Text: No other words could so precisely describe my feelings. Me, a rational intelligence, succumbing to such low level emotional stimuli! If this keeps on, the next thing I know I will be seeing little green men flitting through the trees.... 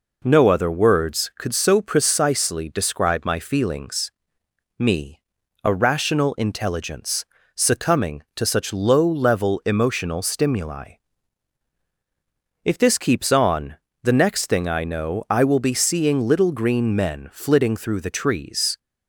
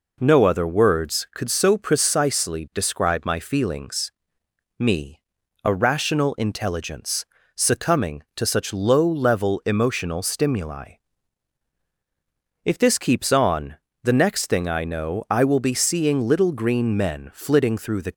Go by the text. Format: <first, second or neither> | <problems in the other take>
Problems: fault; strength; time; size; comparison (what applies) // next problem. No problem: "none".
first | stops before "trees"; at 18.1 s